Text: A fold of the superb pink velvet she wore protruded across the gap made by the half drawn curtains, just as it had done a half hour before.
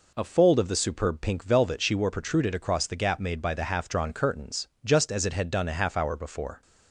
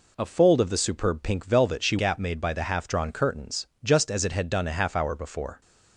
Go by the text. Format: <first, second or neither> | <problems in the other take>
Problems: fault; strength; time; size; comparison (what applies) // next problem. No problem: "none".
first | skips "wore protruded across the"; at 1.9 s